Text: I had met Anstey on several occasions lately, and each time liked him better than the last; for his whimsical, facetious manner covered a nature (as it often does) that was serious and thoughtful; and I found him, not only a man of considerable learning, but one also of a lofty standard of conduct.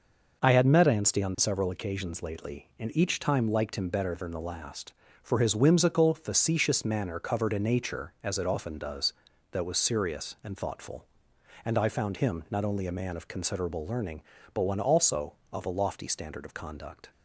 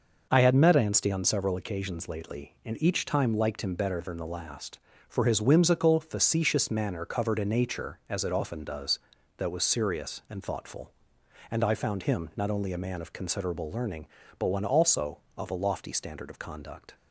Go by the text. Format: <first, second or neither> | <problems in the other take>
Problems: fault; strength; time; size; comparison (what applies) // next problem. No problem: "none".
neither | none